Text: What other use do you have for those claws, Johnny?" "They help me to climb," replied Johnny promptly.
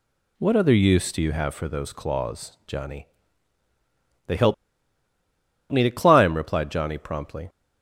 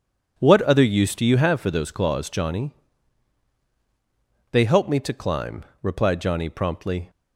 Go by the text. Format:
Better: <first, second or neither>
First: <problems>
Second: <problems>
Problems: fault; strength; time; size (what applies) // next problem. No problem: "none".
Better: second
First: pauses between "help" and "me"; at 4.5 s; 1.1 s long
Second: none